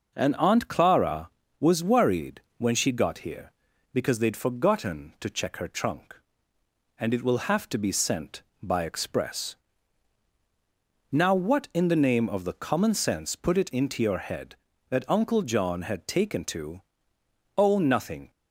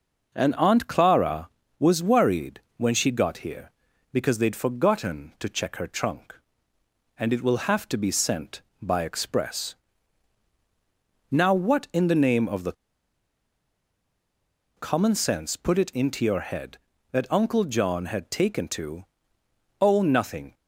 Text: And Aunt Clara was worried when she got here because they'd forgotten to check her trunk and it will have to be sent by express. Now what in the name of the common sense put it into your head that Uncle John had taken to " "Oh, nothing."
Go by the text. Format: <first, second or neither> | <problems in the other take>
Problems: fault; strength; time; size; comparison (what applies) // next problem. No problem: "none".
first | pauses between "worried" and "when"; slight; at 2.6 s; 0.18 s long; slight in the first // pauses between "the" and "common"; strong; at 12.7 s; 2.0 s long